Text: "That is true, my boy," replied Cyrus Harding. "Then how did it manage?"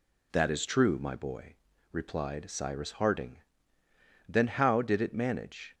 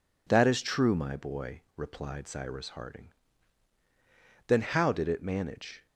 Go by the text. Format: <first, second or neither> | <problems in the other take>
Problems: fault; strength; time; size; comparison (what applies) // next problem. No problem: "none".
neither | none